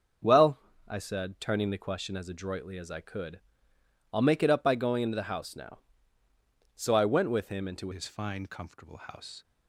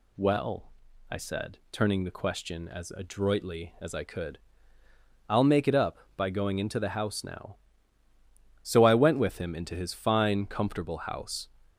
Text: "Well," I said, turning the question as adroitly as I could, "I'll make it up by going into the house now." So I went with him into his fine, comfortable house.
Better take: second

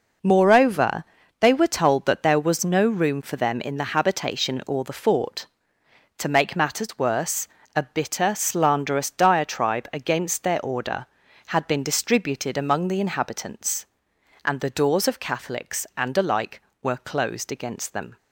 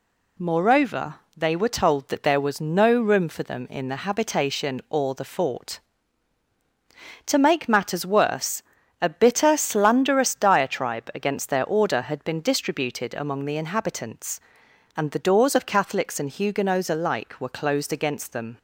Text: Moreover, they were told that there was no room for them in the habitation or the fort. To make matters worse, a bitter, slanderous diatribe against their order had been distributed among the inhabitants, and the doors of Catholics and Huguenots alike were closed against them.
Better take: second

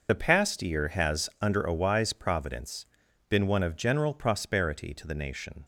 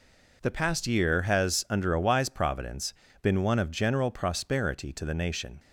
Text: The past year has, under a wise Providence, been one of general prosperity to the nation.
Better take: second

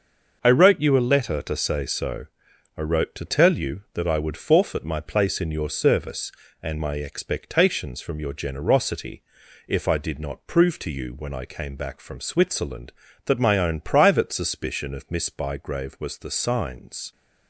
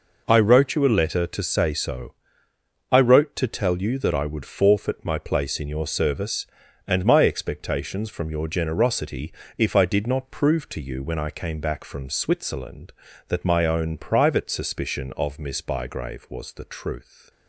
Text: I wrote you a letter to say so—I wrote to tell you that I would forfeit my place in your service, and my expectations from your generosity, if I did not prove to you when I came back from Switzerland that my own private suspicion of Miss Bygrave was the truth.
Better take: second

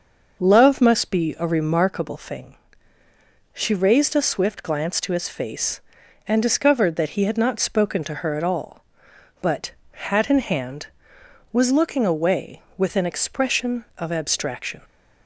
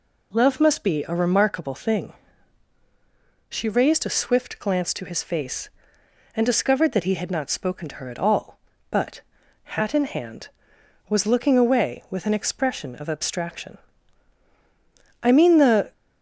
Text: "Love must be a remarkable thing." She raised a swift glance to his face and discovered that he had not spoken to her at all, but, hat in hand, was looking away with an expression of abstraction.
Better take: first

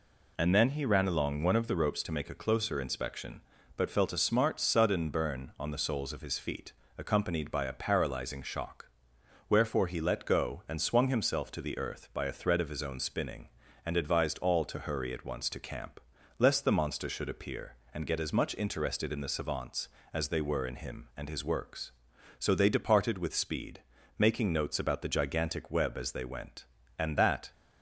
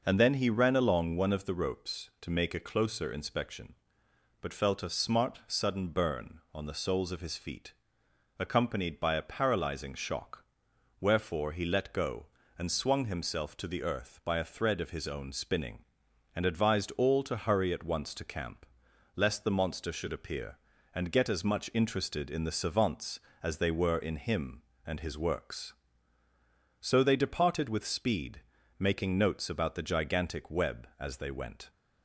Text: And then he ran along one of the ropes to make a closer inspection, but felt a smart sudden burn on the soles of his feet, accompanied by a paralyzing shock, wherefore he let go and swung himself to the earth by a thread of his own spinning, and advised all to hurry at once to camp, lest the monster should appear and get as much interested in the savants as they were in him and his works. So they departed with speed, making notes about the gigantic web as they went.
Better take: second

